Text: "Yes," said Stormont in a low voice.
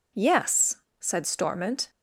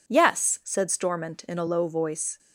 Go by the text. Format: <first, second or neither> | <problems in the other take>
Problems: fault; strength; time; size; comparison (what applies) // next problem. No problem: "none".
second | stops before "in a low voice"; at 1.8 s